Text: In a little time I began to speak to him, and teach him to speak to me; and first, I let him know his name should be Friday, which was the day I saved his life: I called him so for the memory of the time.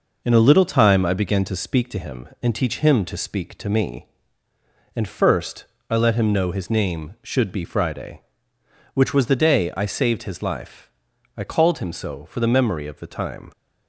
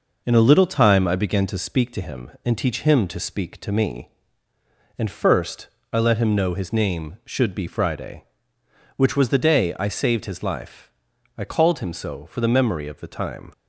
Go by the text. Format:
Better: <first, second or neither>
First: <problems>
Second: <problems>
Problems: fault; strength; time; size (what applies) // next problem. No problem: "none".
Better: neither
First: none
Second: none